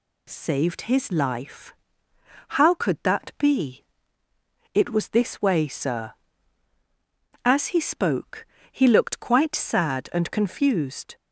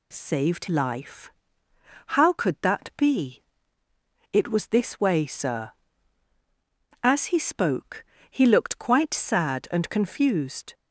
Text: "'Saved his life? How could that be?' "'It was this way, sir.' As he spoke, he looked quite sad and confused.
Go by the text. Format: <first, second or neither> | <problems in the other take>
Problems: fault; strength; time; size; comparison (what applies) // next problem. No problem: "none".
first | skips "his"; at 0.6 s